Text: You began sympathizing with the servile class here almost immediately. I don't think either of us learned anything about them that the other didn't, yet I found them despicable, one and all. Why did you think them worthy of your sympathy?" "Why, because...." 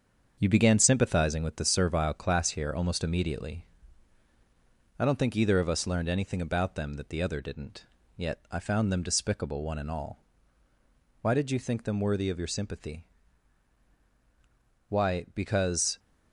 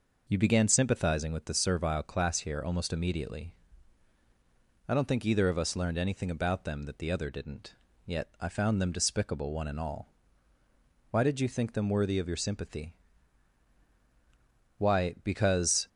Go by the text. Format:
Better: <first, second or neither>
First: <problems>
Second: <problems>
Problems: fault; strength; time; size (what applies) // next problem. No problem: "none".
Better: second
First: gets quieter; noticeable; throughout; 5.5 dB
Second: none